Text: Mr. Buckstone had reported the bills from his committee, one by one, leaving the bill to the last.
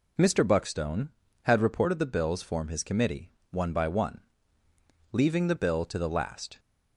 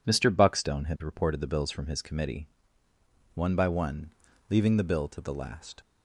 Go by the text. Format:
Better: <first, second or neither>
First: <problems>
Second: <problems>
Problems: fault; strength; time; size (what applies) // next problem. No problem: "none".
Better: second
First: says "form" for "from"; at 2.4 s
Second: none